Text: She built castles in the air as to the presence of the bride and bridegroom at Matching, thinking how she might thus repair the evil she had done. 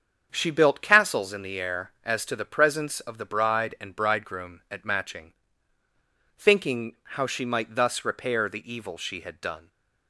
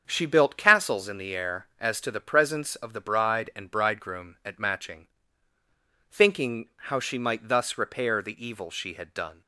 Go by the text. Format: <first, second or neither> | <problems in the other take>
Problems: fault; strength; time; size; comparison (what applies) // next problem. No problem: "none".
neither | starts louder than the rest; strong; the same in both